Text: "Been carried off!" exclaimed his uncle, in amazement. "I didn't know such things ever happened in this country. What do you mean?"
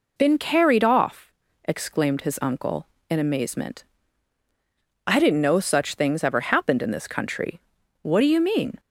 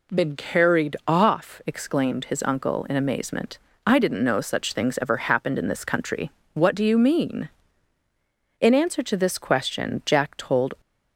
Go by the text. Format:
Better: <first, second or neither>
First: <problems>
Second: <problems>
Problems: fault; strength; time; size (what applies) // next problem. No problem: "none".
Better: first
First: none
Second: goes on to say "In answer to this question Jack told"; strong; from 8.6 s on; 2.1 s long